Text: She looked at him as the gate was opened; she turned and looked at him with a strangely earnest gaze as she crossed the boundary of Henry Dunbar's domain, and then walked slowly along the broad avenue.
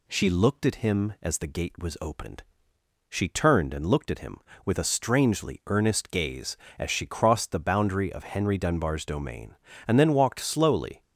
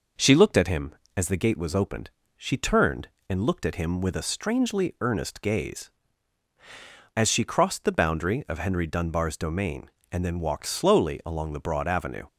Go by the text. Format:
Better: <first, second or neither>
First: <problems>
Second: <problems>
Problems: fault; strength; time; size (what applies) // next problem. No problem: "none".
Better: second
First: stops before "along the broad avenue"; at 11.0 s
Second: none